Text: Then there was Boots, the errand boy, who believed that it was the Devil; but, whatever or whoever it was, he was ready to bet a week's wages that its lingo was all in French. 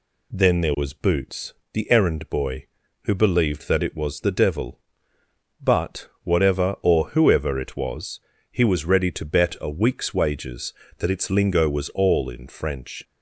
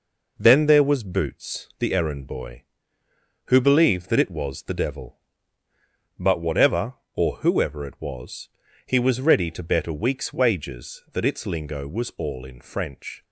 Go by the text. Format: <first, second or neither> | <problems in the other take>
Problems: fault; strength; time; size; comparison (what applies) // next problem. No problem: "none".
neither | none